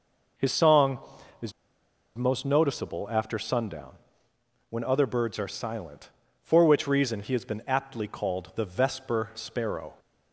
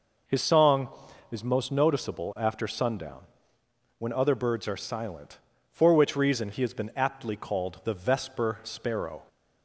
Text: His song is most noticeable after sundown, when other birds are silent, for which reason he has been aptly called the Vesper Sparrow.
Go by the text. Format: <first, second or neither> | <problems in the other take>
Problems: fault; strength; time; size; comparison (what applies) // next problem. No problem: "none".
second | pauses between "is" and "most"; noticeable; at 1.5 s; 0.64 s long